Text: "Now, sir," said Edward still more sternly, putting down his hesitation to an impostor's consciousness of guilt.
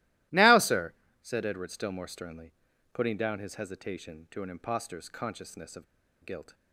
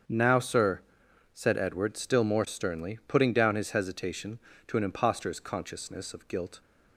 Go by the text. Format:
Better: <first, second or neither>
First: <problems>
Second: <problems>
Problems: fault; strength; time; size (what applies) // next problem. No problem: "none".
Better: second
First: starts louder than the rest; strong; until 1.6 s; 16.5 dB // pauses between "of" and "guilt"; at 5.8 s; 0.38 s long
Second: starts louder than the rest; strong; until 1.6 s; 7 dB